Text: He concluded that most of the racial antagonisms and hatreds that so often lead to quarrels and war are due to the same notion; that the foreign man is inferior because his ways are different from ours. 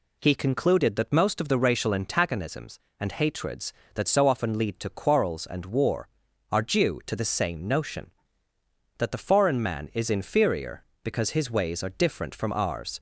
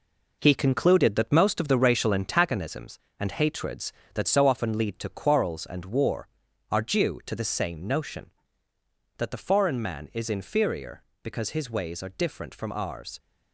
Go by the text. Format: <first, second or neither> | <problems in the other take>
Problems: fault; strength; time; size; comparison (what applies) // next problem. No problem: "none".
first | gets quieter; throughout; 7 dB